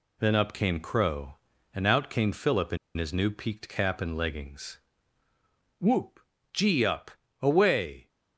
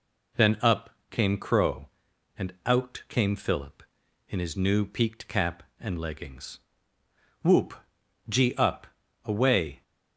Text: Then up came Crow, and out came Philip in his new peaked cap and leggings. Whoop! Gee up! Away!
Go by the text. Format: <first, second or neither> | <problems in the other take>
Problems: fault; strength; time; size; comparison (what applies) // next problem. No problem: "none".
second | pauses between "in" and "his"; slight; at 2.7 s; 0.20 s long